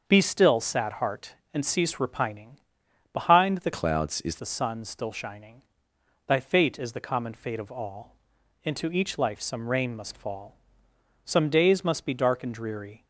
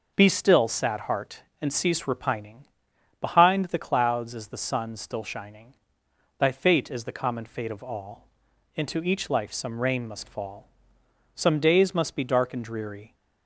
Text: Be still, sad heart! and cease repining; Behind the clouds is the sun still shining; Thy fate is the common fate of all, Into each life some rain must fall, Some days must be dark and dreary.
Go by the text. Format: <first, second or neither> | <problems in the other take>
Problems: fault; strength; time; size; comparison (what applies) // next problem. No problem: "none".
second | starts louder than the rest; until 1.0 s; 6.5 dB // changes voice from "clouds" to "is"; from 3.7 to 4.3 s; 0.6 s long